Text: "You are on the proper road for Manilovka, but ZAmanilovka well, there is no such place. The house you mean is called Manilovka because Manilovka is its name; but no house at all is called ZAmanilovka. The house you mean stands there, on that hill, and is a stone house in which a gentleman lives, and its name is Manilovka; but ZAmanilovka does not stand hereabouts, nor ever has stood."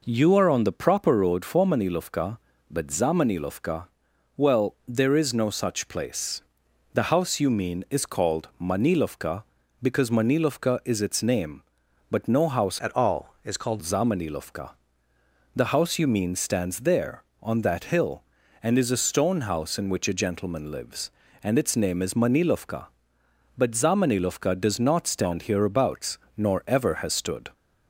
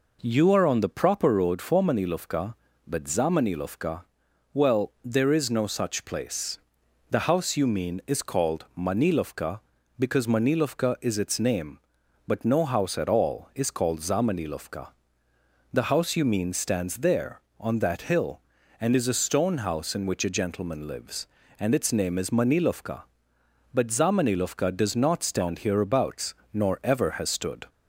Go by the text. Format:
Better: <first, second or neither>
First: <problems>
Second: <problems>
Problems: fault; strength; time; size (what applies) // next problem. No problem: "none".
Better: second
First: pauses between "ZAmanilovka" and "well"; noticeable; at 3.8 s; 0.48 s long // changes voice from "at" to "called"; from 12.8 to 13.7 s; 0.9 s long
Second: pauses between "ZAmanilovka" and "well"; noticeable; at 4.0 s; 0.48 s long